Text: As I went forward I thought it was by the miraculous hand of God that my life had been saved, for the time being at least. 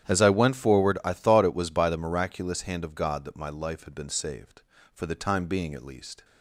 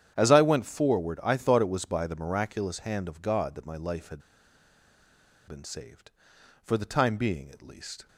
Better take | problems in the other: first | starts louder than the rest; strong; until 1.1 s; 9.5 dB; strong in the first // pauses between "had" and "been"; strong; at 4.2 s; 1.2 s long

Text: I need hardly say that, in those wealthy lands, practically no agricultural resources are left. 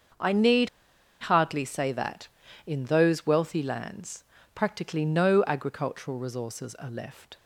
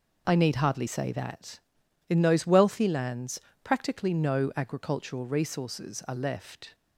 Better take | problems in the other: second | starts louder than the rest; until 1.7 s; 6.5 dB // pauses between "need" and "hardly"; noticeable; at 0.6 s; 0.53 s long

